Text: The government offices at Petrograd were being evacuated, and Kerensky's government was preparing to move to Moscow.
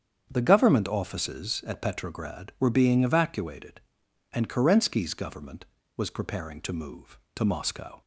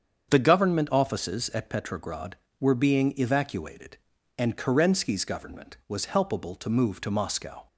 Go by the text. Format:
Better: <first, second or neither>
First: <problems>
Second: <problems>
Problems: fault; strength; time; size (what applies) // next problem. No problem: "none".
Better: first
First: starts louder than the rest; strong; until 1.3 s; 8 dB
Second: starts louder than the rest; strong; until 1.3 s; 7.5 dB // says "helpable" for "preparing"; at 6.0 s